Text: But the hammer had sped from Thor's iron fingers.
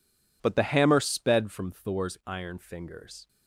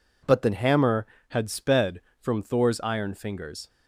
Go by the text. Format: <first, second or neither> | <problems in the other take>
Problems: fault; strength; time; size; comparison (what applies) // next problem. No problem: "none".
second | skips "had"; at 0.9 s